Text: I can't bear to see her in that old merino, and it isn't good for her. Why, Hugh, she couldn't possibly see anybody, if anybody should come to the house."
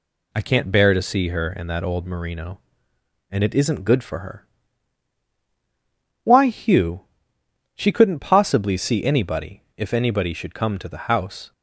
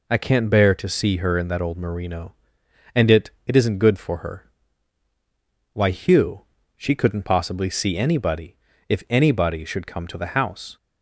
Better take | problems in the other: first | says "it" twice; at 3.4 s

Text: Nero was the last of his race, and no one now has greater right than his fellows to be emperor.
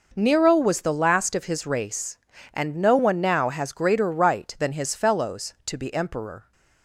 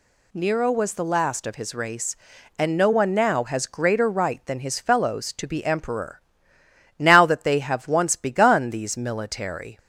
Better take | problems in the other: first | goes on to say "Now that they have once begun these military"; strong; from 6.9 s on; 2.8 s long

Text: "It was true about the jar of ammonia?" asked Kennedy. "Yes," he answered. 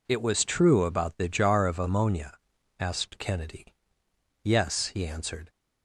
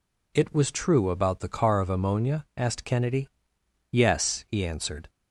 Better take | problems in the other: first | says "car" for "jar"; at 1.4 s

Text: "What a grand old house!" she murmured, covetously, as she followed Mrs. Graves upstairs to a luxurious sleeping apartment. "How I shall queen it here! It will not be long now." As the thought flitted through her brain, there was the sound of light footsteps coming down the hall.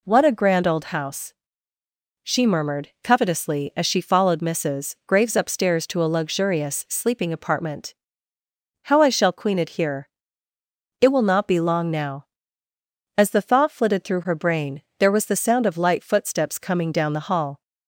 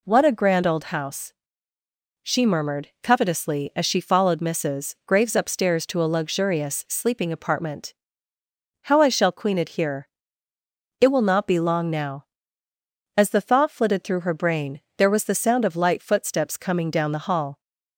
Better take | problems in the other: neither | none

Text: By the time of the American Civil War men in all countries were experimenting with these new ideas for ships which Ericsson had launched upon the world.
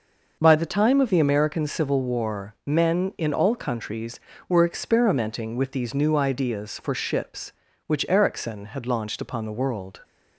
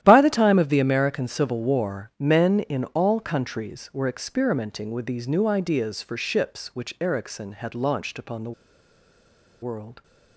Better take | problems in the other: first | starts louder than the rest; strong; until 1.0 s; 11.5 dB // pauses between "the" and "world"; at 8.5 s; 1.1 s long

